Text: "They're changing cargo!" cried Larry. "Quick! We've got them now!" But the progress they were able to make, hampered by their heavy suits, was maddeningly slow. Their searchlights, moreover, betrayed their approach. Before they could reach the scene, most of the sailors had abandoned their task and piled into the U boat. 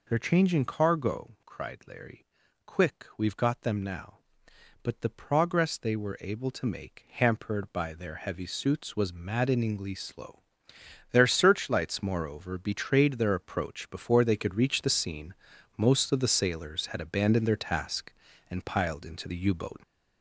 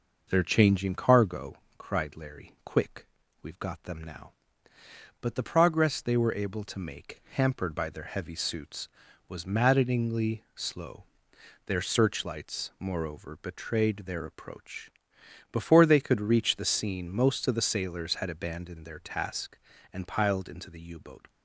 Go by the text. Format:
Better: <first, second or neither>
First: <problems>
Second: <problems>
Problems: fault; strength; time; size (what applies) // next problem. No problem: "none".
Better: second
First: gets louder; noticeable; throughout; 5.5 dB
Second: none